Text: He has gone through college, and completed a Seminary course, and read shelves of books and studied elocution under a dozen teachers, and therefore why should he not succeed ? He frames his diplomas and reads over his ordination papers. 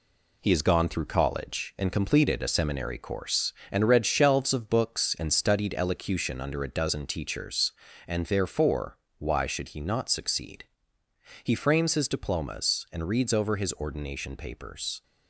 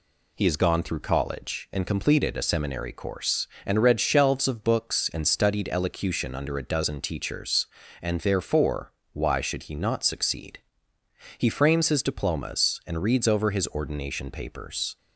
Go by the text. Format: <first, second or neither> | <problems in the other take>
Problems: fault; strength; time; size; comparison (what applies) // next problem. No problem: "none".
second | gets quieter; noticeable; throughout; 5 dB // pauses between "therefore" and "why"; slight; at 8.9 s; 0.22 s long; slight in the second